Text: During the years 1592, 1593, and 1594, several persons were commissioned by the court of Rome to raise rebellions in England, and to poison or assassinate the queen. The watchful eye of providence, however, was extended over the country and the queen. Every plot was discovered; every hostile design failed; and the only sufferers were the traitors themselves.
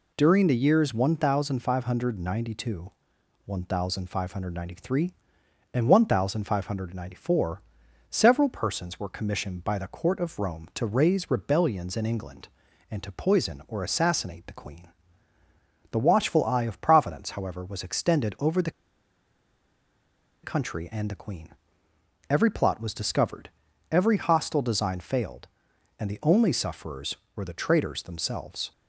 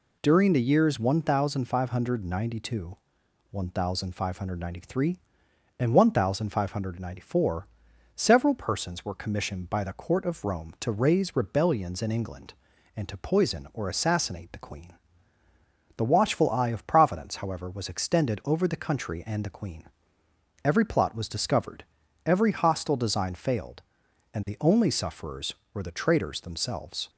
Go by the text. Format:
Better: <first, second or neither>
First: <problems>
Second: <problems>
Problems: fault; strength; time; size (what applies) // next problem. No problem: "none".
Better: second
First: pauses between "the" and "country"; strong; at 18.7 s; 1.7 s long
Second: none